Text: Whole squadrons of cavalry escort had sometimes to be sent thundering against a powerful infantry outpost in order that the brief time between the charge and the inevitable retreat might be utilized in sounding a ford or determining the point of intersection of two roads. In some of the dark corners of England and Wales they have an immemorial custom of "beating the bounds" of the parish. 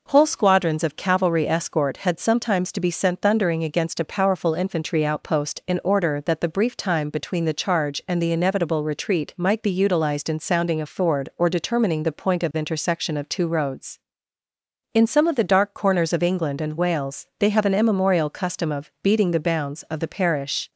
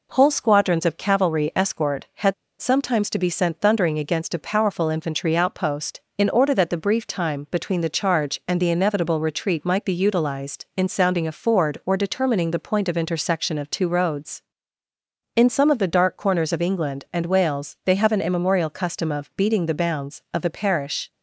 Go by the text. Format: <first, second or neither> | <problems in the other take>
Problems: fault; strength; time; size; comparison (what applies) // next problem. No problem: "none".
first | pauses between "had" and "sometimes"; slight; at 2.3 s; 0.26 s long